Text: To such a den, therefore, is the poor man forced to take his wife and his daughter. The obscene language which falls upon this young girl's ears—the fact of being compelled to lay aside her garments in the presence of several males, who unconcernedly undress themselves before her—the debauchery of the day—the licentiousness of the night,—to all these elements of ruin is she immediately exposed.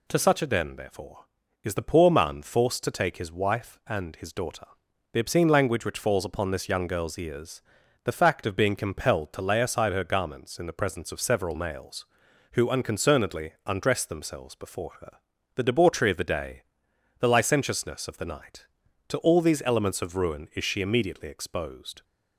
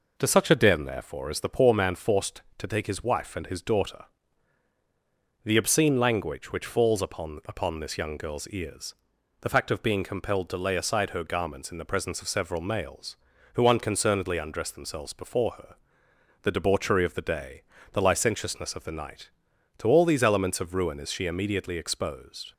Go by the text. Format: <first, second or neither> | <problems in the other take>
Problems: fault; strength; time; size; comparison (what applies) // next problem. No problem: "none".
first | says "upon" twice; at 7.4 s